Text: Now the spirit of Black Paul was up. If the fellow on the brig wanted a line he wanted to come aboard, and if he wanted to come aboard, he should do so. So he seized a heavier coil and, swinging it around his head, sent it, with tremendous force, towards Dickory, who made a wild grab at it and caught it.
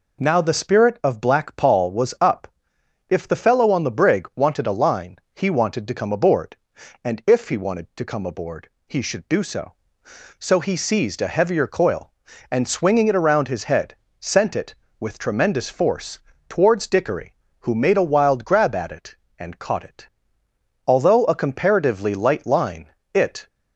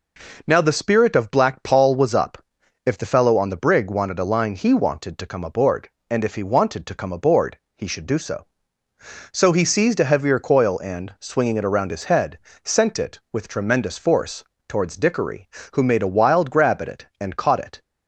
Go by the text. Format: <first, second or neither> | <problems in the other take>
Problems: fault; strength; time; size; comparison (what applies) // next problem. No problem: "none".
second | pauses between "line" and "he"; slight; at 5.1 s; 0.16 s long // goes on to say "Although a comparatively light line it"; strong; from 20.8 s on; 2.6 s long